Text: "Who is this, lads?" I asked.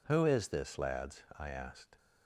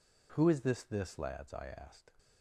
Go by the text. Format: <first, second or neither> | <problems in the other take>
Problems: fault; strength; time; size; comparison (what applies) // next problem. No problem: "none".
first | says "this" twice; at 0.8 s